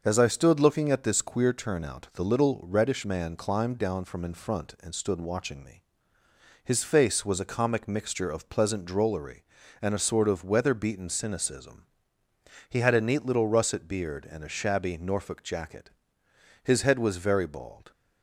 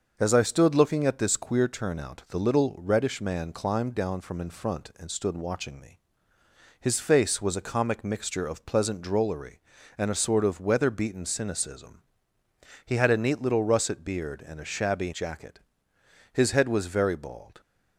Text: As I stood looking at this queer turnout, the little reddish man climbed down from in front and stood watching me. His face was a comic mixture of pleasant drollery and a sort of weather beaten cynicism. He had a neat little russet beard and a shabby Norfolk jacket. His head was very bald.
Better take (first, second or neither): first